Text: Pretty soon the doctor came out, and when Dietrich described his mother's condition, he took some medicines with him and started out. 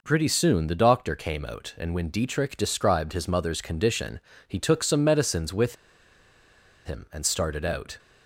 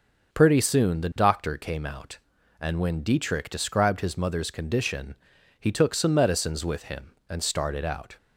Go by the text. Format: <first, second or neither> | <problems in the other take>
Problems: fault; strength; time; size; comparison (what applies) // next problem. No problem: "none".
second | pauses between "with" and "him"; at 5.7 s; 1.1 s long